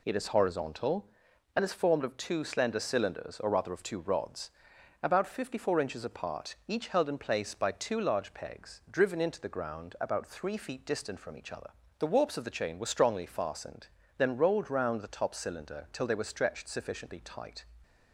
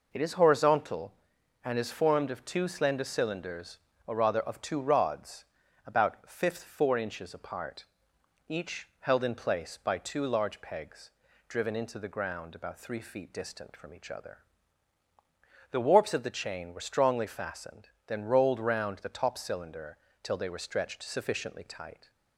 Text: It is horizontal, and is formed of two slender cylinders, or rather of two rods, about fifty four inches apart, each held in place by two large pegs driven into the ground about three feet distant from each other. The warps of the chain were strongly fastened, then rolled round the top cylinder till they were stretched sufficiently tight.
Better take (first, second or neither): first